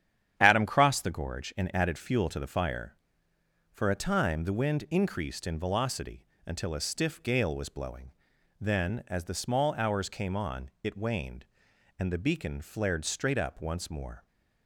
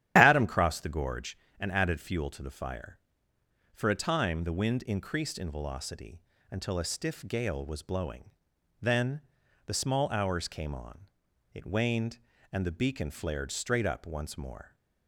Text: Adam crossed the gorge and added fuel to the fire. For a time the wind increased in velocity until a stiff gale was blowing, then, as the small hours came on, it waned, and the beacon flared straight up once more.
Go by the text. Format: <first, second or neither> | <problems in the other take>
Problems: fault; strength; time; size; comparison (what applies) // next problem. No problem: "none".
first | starts louder than the rest; strong; until 1.1 s; 11 dB; strong in the first // pauses between "velocity" and "until"; slight; at 6.2 s; 0.28 s long; slight in the first // skips "as"; at 9.4 s